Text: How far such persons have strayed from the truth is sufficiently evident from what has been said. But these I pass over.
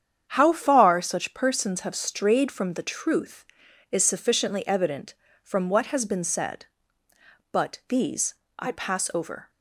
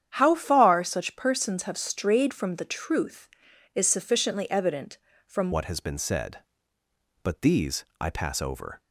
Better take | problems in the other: first | starts louder than the rest; strong; until 1.1 s; 9 dB; strong in the first // changes voice at "what"; from 5.5 s on; 3.3 s long // pauses between "these" and "I"; slight; at 7.8 s; 0.16 s long; slight in the first

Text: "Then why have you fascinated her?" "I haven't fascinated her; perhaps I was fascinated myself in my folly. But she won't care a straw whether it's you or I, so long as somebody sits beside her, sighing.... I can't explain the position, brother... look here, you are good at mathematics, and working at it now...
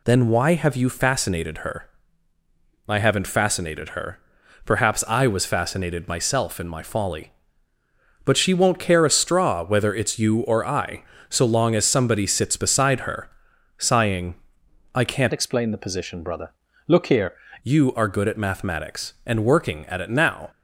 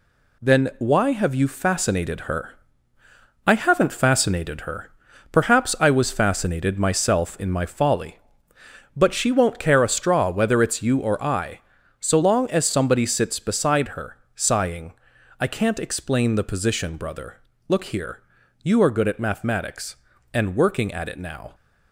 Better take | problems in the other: second | changes voice from "explain" to "here"; from 15.3 to 17.3 s; 2.0 s long

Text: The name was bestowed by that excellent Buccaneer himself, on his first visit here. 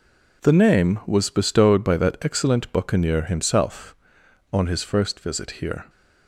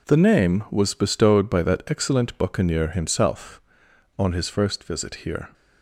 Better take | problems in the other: neither | none

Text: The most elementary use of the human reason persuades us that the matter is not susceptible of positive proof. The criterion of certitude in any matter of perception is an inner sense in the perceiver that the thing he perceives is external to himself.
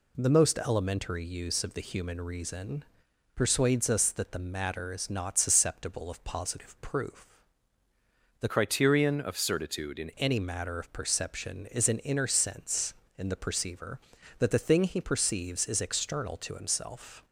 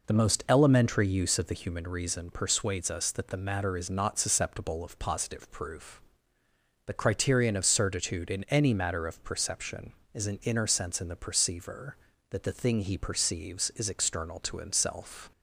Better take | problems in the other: second | pauses between "reason" and "persuades"; noticeable; at 2.8 s; 0.48 s long // changes voice from "criterion" to "in"; from 8.4 to 10.0 s; 1.6 s long

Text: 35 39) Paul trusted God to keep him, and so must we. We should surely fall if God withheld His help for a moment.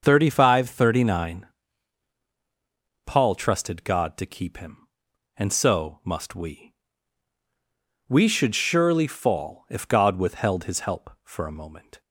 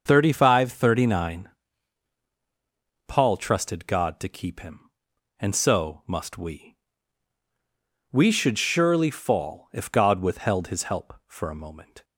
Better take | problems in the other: neither | starts louder than the rest; the same in both

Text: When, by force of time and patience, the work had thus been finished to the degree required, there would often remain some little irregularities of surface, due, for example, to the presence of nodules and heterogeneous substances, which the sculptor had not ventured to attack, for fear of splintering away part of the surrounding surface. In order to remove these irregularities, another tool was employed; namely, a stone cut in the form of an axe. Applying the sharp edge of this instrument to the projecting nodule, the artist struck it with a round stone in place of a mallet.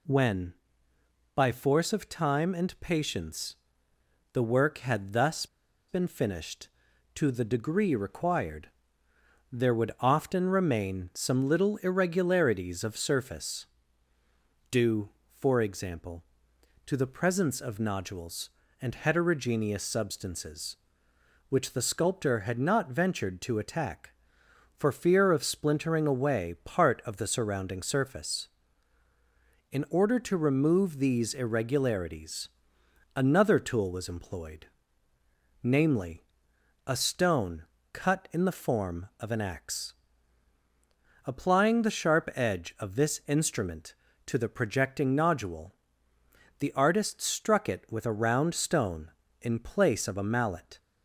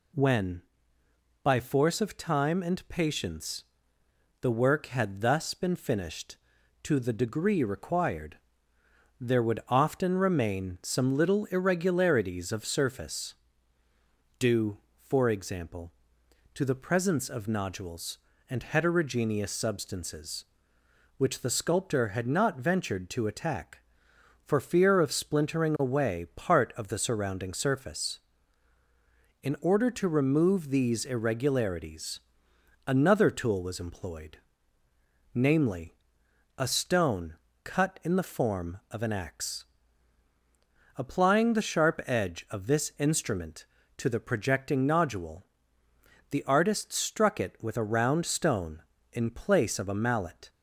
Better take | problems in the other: second | pauses between "thus" and "been"; at 5.4 s; 0.42 s long // pauses between "stone" and "cut"; slight; at 37.6 s; 0.28 s long; slight in the second

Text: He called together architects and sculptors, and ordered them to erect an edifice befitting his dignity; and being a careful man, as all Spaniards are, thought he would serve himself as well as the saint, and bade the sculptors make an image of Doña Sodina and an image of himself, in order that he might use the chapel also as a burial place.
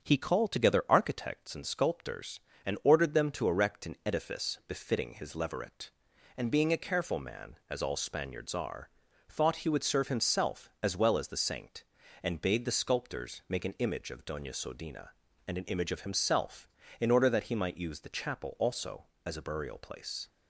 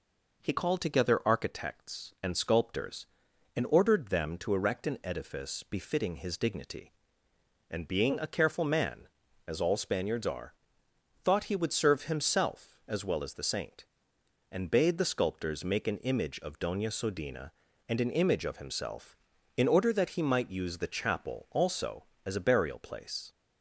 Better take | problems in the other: second | starts louder than the rest; until 1.0 s; 7 dB // says "leveret" for "dignity"; at 5.3 s

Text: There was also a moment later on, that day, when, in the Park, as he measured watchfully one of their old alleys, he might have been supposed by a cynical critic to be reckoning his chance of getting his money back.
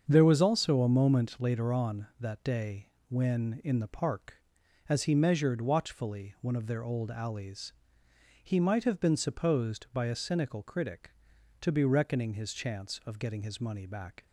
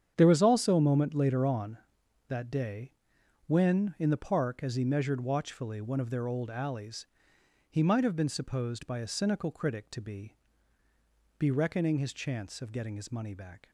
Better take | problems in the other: first | starts louder than the rest; strong; until 1.1 s; 8.5 dB; also in the first // says "be" twice; at 11.3 s

